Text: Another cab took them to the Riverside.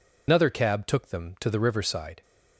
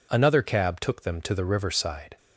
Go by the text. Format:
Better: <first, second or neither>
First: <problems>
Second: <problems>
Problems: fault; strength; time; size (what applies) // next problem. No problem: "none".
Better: second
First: loses the start of "Another"; at 0.2 s; 105 ms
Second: none